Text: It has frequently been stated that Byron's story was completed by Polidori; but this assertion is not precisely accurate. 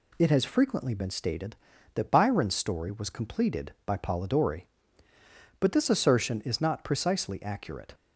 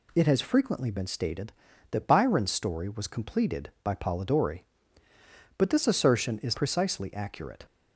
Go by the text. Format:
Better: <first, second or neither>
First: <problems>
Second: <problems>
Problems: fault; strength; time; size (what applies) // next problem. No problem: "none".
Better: first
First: none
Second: skips "not"; at 6.5 s